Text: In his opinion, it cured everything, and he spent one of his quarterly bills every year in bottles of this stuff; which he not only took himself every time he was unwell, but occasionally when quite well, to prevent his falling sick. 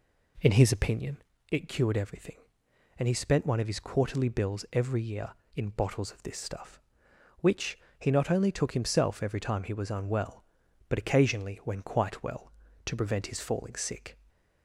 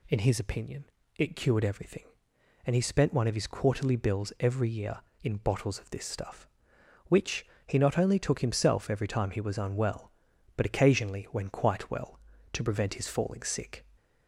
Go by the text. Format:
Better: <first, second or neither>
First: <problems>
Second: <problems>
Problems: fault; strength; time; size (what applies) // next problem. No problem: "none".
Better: second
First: starts louder than the rest; slight; until 1.3 s; 2.5 dB // pauses between "which" and "he"; slight; at 7.7 s; 0.20 s long // stays silent after the last word; slight; from 14.1 s on; 0.5 s long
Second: pauses between "which" and "he"; slight; at 7.4 s; 0.20 s long